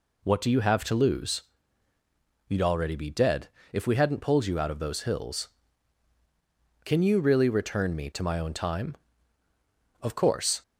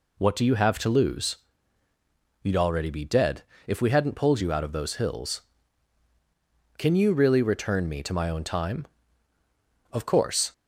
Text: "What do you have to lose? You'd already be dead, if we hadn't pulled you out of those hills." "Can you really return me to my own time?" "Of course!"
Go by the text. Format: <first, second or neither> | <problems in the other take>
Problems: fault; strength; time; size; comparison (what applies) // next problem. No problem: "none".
neither | none